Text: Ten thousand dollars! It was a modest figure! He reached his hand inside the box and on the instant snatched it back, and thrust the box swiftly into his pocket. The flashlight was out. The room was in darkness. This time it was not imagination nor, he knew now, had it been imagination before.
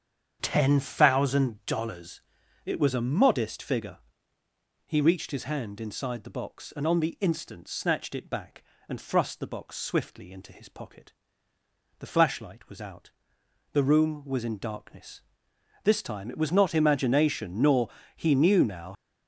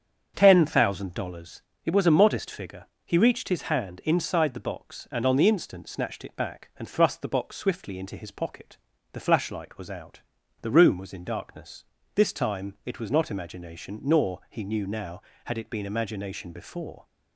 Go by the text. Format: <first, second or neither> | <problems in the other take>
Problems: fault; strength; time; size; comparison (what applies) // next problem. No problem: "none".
second | starts louder than the rest; strong; until 1.4 s; 7.5 dB; strong in the second // stops before "had it been imagination before"; at 18.9 s